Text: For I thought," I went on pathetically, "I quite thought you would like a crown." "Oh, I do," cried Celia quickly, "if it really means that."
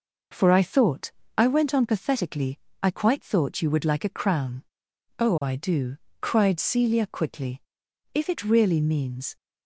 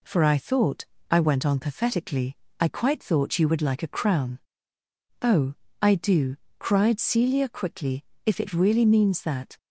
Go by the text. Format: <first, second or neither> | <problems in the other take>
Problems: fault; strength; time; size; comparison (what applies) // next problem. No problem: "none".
second | stops before "that"; at 9.3 s